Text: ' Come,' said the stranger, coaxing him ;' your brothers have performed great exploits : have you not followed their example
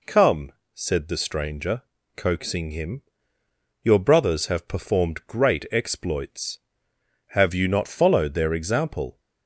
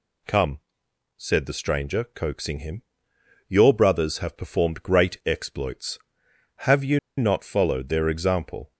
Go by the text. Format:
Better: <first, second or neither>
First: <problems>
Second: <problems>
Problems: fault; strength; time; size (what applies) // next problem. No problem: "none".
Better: first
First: none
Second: pauses between "you" and "not"; slight; at 6.9 s; 0.19 s long